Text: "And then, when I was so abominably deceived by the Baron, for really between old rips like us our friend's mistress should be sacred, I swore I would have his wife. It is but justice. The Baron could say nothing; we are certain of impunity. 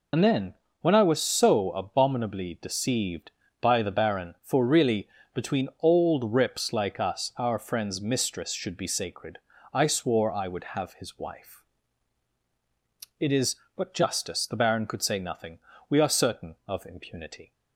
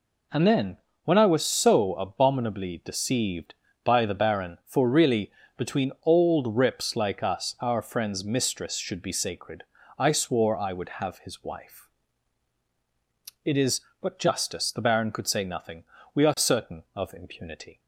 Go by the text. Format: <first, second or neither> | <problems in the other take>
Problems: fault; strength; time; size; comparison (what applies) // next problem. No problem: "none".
second | loses the start of "And"; at 0.1 s; 50 ms // pauses between "really" and "between"; slight; at 5.0 s; 0.26 s long; slight in the second